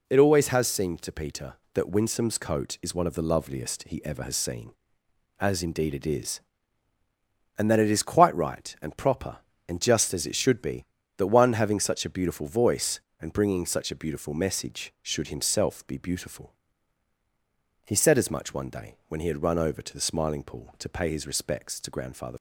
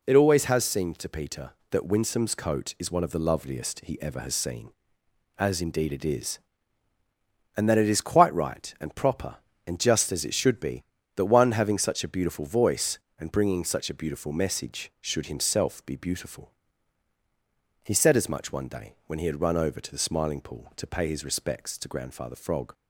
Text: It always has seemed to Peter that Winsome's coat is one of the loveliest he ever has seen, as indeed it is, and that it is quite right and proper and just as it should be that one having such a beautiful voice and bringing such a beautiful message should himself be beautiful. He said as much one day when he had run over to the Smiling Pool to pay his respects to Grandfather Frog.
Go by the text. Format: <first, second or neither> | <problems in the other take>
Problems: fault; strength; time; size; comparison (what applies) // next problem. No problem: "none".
second | stops before "Frog"; at 22.3 s